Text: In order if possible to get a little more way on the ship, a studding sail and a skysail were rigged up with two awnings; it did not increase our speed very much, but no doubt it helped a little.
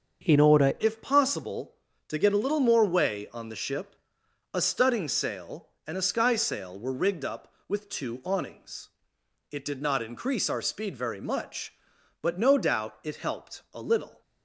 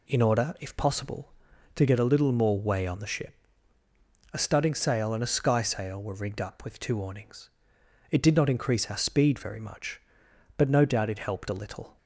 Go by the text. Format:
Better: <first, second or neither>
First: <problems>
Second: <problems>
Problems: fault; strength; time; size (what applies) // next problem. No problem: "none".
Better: second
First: starts louder than the rest; until 1.3 s; 7 dB // changes voice at "if"; from 0.7 s on; 13.5 s long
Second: none